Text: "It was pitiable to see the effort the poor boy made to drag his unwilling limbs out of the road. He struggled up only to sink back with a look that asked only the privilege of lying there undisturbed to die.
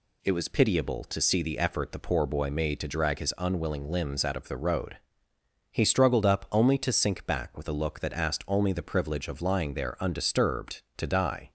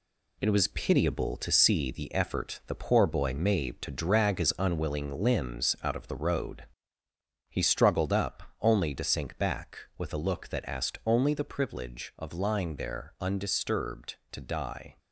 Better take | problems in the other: first | gets quieter; noticeable; throughout; 5 dB // pauses between "up" and "only"; slight; at 8.4 s; 0.18 s long

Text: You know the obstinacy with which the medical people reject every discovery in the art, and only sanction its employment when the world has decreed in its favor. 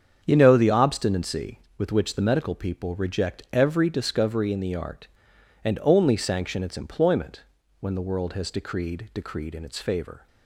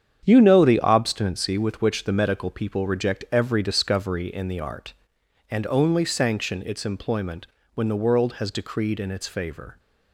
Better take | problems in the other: second | starts louder than the rest; strong; until 1.2 s; 7 dB; strong in the second // pauses between "employment" and "when"; at 7.4 s; 0.38 s long; slight in the second // says "decreed" twice; at 9.1 s

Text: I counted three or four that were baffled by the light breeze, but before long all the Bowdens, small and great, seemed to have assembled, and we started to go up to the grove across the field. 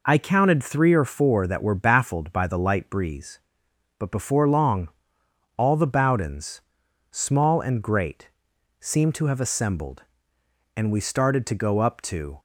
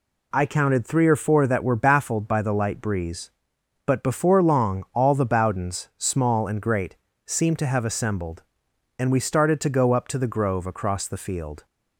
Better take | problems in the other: second | pauses between "long" and "all"; noticeable; at 4.8 s; 0.70 s long // stops before "the grove across the field"; at 12.3 s

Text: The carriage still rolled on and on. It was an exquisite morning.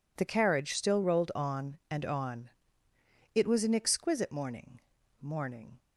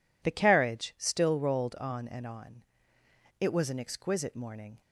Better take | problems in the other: second | says "morning" twice; at 5.2 s

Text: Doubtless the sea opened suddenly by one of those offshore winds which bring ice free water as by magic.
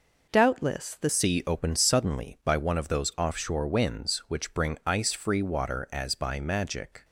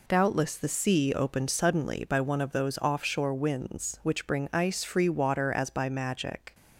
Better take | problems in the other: second | changes voice at "sea"; from 1.0 s on; 6.0 s long

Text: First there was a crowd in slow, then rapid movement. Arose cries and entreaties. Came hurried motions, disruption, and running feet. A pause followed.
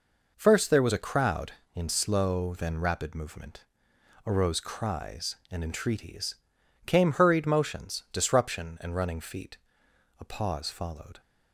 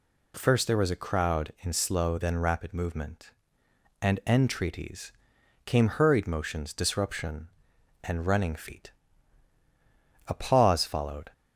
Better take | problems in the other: first | skips "Arose cries"; at 3.6 s

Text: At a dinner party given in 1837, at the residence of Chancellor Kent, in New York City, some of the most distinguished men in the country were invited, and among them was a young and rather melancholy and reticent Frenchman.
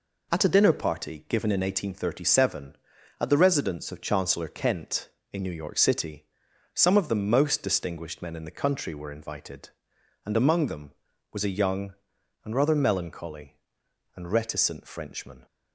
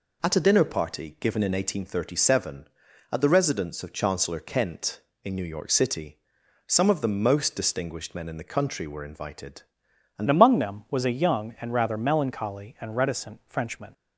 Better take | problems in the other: first | changes voice at "among"; from 10.2 s on; 3.7 s long

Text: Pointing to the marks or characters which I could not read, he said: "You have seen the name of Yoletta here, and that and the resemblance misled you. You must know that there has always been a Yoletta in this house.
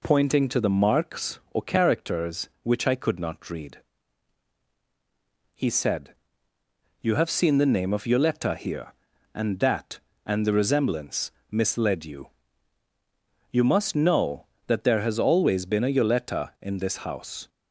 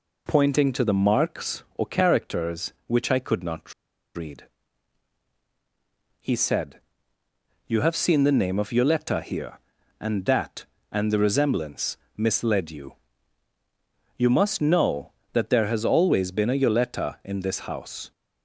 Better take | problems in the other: first | pauses between "not" and "read"; at 3.7 s; 0.41 s long // pauses between "resemblance" and "misled"; slight; at 11.9 s; 0.18 s long; slight in the first

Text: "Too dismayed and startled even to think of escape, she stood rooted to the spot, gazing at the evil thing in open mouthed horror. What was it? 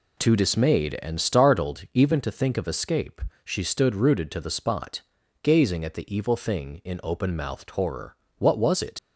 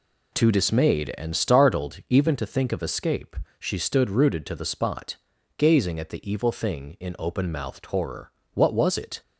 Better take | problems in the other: second | leaves "it" unfinished; at 8.9 s; 70 ms

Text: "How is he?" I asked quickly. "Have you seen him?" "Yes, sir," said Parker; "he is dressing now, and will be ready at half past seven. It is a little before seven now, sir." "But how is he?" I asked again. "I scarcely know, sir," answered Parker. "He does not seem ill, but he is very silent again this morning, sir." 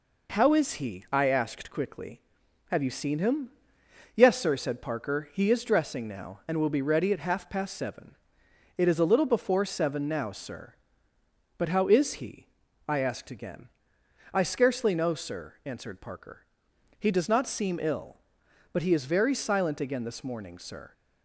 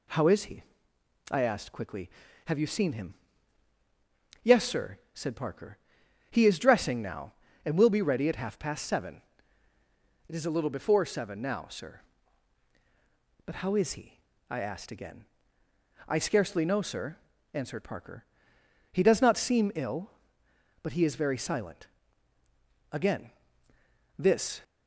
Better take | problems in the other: first | pauses between "silent" and "again"; at 21.8 s; 1.0 s long // pauses between "again" and "this"; noticeable; at 23.2 s; 0.88 s long // stops before "morning sir"; at 24.6 s

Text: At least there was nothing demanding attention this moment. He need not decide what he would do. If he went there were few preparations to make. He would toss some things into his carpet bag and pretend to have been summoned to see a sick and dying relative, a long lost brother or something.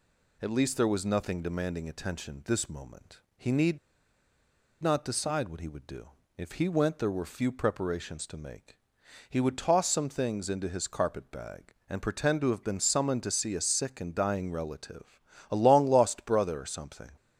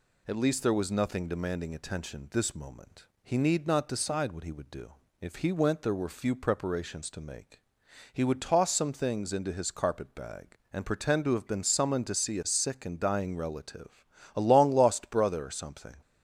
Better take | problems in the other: second | pauses between "need" and "not"; at 3.7 s; 1.0 s long

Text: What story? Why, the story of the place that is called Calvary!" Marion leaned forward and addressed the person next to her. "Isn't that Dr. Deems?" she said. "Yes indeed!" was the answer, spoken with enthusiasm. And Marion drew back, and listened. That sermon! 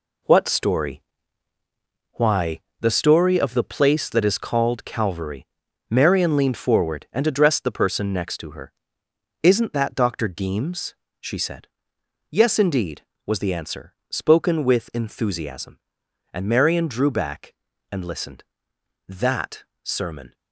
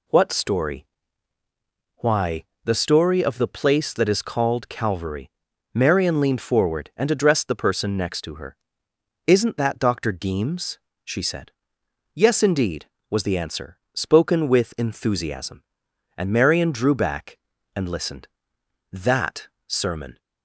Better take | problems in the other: second | gets quieter; strong; throughout; 8.5 dB // pauses between "That" and "sermon"; slight; at 19.6 s; 0.18 s long; slight in the second

